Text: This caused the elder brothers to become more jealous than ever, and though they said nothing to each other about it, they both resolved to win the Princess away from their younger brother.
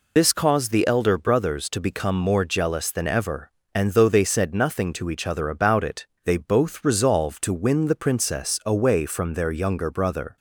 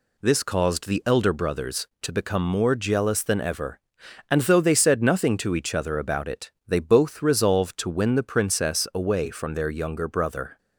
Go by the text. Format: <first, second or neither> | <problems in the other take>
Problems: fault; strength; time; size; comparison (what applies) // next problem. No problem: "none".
second | loses the start of "This"; at 0.1 s; 75 ms